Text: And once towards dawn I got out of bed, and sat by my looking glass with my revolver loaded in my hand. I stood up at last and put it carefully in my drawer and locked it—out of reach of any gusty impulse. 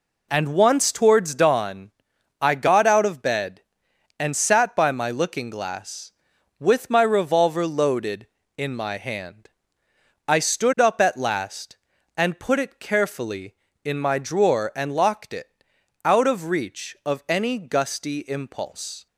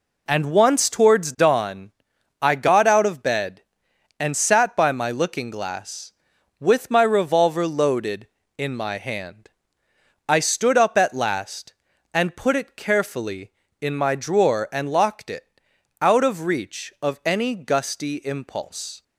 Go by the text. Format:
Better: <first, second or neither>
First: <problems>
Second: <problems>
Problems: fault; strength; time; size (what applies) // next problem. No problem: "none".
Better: neither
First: pauses between "dawn" and "I"; noticeable; at 1.9 s; 0.50 s long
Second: pauses between "dawn" and "I"; noticeable; at 1.9 s; 0.50 s long